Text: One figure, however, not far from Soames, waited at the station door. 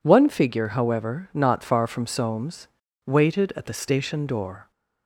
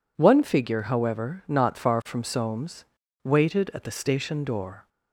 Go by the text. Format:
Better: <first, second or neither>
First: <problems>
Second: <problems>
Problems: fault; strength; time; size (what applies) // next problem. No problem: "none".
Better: neither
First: none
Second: none